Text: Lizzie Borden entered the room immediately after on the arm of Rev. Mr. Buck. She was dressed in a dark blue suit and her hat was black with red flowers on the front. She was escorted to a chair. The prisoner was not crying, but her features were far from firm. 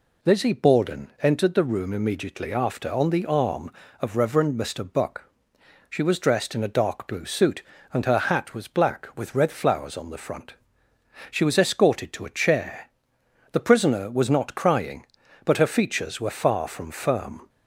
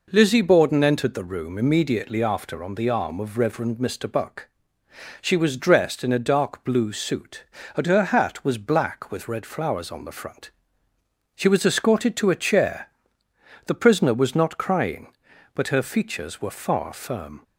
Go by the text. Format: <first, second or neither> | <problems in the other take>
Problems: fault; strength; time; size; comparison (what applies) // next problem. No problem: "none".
first | skips "from"; at 16.9 s